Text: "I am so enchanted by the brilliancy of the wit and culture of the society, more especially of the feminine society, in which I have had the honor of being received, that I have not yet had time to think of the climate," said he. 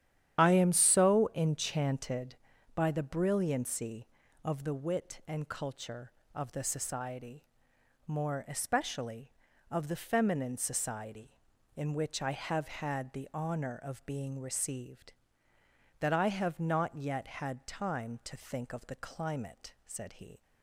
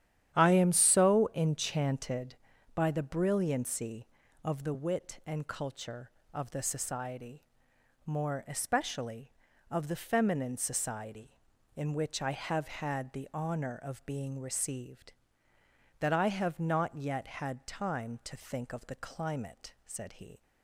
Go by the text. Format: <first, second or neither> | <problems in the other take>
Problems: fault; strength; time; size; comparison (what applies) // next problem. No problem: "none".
second | loses the start of "I"; at 0.3 s; 35 ms // starts louder than the rest; strong; until 1.4 s; 10.5 dB; strong in the second